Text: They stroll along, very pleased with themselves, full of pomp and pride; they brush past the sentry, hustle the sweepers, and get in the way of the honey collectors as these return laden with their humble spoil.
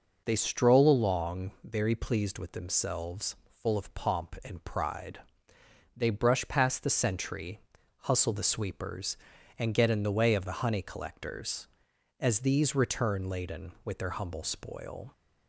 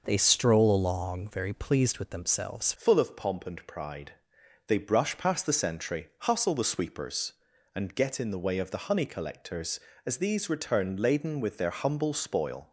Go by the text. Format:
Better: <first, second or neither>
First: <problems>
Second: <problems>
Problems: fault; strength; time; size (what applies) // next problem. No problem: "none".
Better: first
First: none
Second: changes voice at "full"; from 2.7 s on; 10.0 s long